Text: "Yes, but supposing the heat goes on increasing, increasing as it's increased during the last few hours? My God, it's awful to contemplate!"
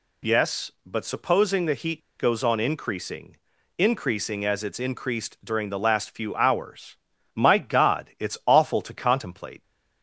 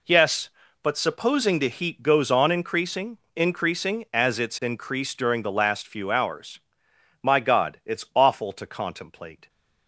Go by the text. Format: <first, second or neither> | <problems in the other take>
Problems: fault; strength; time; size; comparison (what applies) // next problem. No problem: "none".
second | pauses between "heat" and "goes"; slight; at 1.9 s; 0.18 s long